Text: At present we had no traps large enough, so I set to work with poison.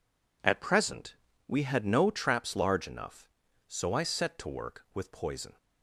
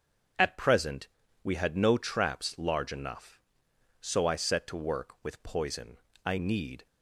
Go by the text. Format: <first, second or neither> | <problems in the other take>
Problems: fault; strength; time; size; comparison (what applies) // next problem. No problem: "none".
first | starts louder than the rest; until 1.7 s; 7 dB // pauses between "present" and "we"; at 1.0 s; 0.38 s long; slight in the first // goes on to say "I need"; from 6.2 s on; 0.60 s long